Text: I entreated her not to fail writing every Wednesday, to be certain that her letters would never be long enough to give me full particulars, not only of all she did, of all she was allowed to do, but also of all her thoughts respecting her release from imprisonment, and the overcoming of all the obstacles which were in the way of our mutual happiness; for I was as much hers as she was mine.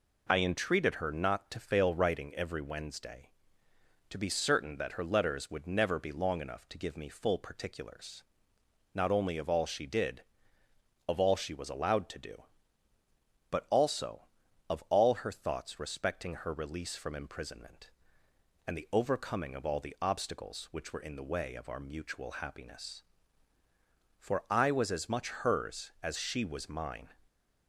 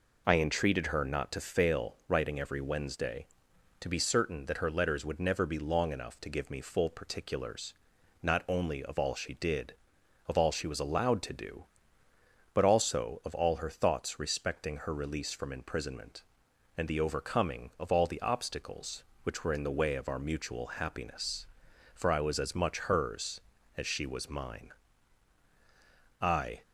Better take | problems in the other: first | goes on to say "I"; slight; from 26.1 s on; 0.42 s long

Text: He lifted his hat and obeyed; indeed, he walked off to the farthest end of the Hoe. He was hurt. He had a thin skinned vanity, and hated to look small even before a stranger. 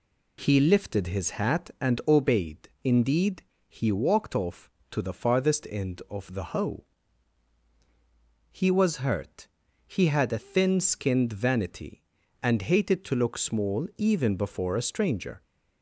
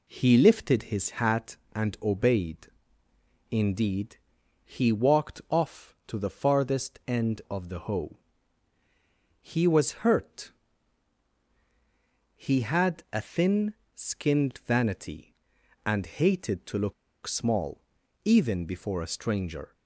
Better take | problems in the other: first | pauses between "thin" and "skinned"; slight; at 13.7 s; 0.20 s long // pauses between "look" and "small"; slight; at 16.9 s; 0.32 s long // pauses between "small" and "even"; at 17.8 s; 0.42 s long

